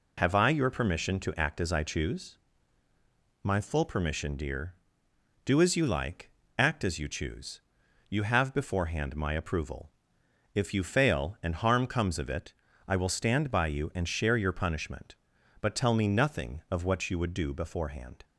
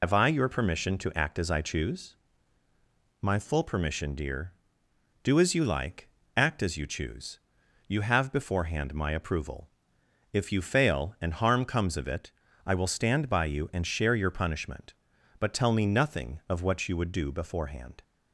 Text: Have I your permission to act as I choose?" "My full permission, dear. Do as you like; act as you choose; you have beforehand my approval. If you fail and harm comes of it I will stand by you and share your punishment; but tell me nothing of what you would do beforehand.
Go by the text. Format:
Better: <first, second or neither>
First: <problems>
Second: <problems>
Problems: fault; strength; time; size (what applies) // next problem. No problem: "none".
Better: first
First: pauses between "it" and "I"; slight; at 12.5 s; 0.36 s long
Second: loses the start of "Have"; at 0.0 s; 65 ms // pauses between "it" and "I"; slight; at 12.3 s; 0.36 s long